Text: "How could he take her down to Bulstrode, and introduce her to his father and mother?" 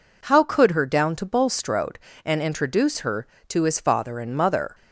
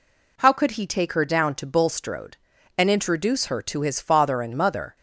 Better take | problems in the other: second | skips "he take"; at 0.7 s

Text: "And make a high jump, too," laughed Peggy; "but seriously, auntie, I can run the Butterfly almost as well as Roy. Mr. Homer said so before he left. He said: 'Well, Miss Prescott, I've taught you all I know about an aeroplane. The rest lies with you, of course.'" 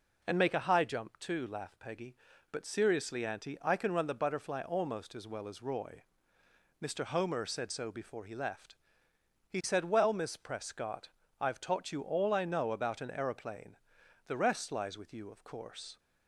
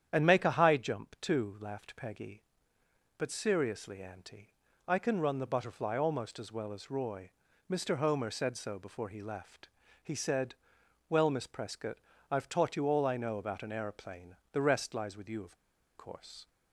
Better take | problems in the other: first | starts louder than the rest; strong; until 1.1 s; 9.5 dB // pauses between "of" and "course"; at 15.5 s; 0.40 s long

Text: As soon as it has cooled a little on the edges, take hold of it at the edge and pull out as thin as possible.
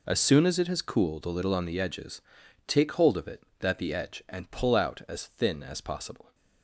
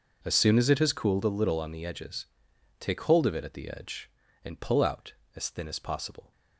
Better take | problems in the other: second | says "that" for "at"; at 3.6 s

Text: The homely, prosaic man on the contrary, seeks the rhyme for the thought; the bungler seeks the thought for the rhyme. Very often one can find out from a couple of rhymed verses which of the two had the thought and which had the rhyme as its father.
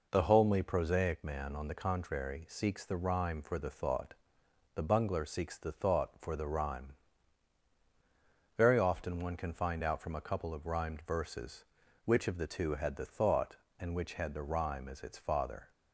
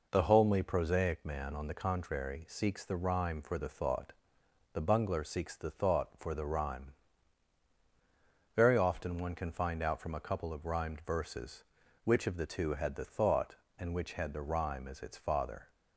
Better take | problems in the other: neither | none

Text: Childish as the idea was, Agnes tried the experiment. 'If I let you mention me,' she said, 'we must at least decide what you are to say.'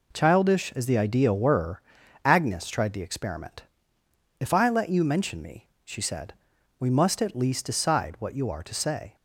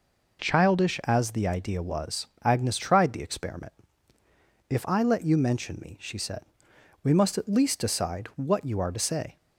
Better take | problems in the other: second | says "were" for "was"; at 1.3 s

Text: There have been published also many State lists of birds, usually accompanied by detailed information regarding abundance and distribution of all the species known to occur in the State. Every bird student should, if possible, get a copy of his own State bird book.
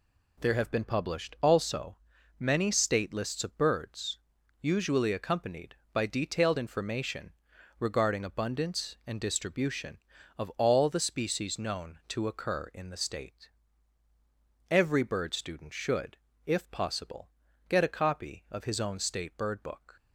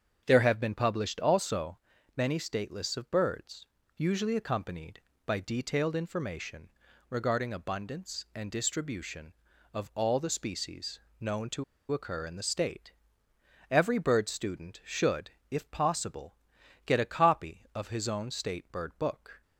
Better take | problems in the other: first | starts louder than the rest; strong; until 1.2 s; 7.5 dB // pauses between "also" and "many"; slight; at 1.7 s; 0.36 s long; also in the first // pauses between "information" and "regarding"; at 6.6 s; 0.40 s long; noticeable in the first // pauses between "species" and "known"; slight; at 11.0 s; 0.18 s long // pauses between "to" and "occur"; slight; at 11.6 s; 0.27 s long

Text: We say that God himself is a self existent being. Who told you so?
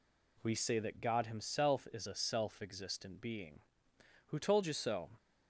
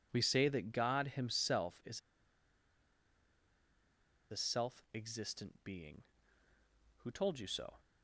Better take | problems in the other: first | pauses between "is" and "a"; strong; at 2.0 s; 2.3 s long

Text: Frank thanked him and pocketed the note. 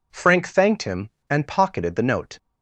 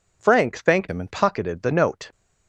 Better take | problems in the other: first | changes voice from "him" to "and"; from 0.8 to 1.0 s; 0.2 s long

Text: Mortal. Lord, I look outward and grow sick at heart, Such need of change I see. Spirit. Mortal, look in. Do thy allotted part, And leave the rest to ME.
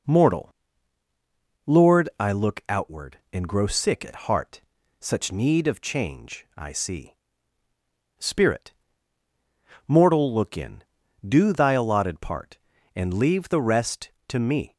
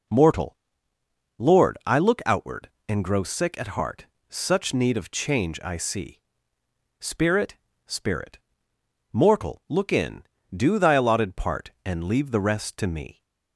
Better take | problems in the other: first | says "Spirit" twice; at 7.8 s

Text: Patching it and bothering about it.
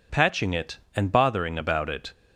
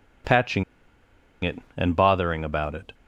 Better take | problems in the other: first | pauses between "Patching" and "it"; noticeable; at 0.6 s; 0.80 s long

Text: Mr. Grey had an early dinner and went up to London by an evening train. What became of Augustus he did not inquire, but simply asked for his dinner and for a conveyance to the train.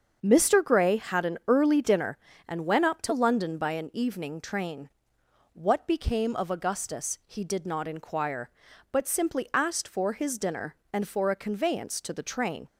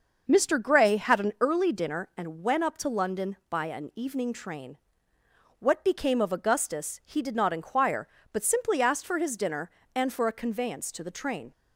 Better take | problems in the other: neither | starts louder than the rest; the same in both

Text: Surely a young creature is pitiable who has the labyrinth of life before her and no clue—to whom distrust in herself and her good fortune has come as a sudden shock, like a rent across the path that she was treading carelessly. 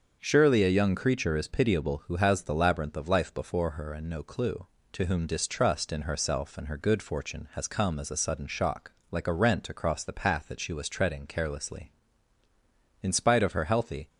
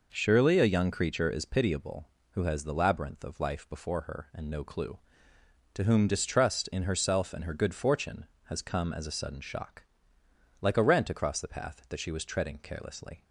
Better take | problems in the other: second | starts louder than the rest; until 1.2 s; 7 dB // goes on to say "In spite of her healthy"; noticeable; from 13.0 s on; 1.0 s long

